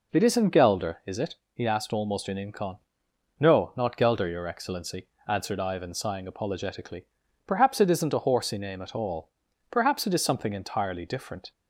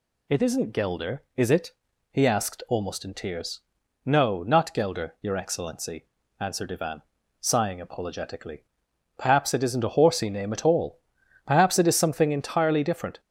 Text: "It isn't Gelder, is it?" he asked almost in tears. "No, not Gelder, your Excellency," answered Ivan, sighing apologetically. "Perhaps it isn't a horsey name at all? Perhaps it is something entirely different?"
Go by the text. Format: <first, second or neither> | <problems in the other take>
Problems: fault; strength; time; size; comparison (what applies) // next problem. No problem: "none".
second | says "incon" for "tears"; at 2.5 s